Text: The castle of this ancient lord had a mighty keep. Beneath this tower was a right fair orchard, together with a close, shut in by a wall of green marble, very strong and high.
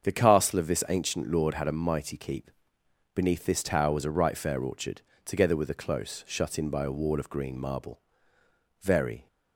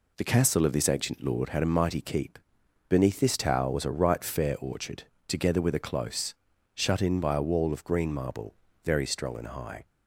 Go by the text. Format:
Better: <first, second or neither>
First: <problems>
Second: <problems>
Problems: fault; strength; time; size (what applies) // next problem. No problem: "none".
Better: second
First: starts louder than the rest; until 1.0 s; 7 dB // stops before "strong and high"; at 9.2 s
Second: none